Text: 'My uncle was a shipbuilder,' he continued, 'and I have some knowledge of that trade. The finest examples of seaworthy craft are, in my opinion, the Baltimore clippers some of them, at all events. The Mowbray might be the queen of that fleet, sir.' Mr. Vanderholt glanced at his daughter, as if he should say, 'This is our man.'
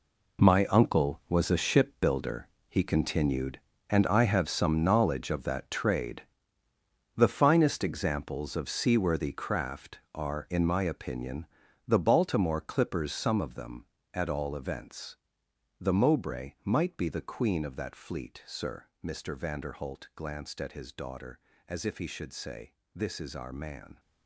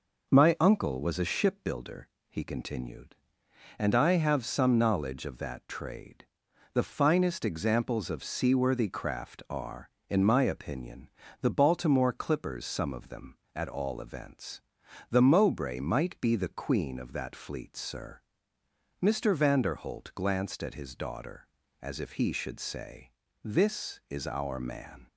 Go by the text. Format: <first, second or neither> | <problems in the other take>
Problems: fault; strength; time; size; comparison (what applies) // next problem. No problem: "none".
second | gets quieter; strong; throughout; 11.5 dB